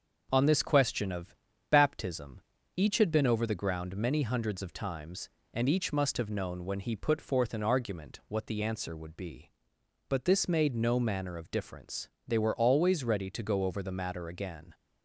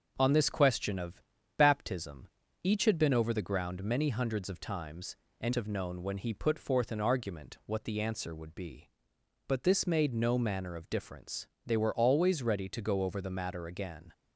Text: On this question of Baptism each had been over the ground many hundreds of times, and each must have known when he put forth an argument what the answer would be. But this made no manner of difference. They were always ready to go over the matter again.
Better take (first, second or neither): first